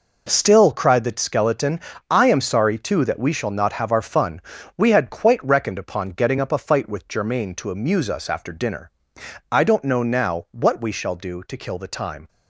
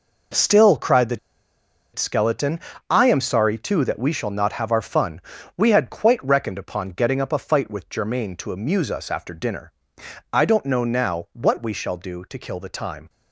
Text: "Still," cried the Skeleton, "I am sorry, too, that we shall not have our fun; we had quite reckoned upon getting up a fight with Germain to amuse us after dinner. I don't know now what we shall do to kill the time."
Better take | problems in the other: first | pauses between "the" and "Skeleton"; noticeable; at 1.1 s; 0.76 s long

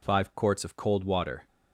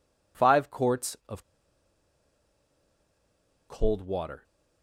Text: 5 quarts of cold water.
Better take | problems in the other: first | pauses between "of" and "cold"; strong; at 1.4 s; 2.2 s long

